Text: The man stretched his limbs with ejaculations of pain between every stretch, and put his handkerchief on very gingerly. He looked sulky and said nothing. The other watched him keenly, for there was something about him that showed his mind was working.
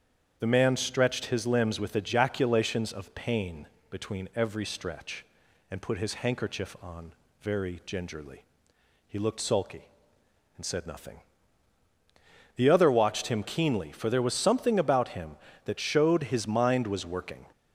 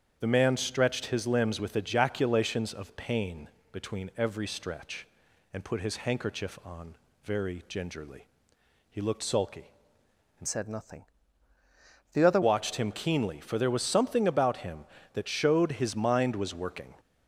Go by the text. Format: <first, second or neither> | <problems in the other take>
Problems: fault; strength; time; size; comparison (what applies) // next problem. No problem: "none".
first | starts louder than the rest; strong; until 1.2 s; 8 dB; strong in the first // pauses between "pain" and "between"; slight; at 3.4 s; 0.22 s long; slight in the first // pauses between "on" and "very"; slight; at 6.9 s; 0.28 s long; slight in the first // changes voice from "said" to "other"; from 10.4 to 12.4 s; 2.0 s long